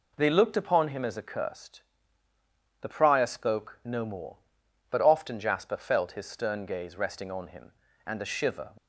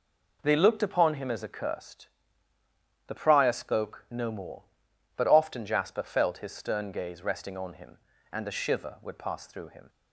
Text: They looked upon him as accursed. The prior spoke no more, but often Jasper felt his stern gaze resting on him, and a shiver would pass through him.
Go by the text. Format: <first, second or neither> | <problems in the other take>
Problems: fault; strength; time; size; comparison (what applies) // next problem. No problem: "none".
second | stops before "would pass through him"; at 8.7 s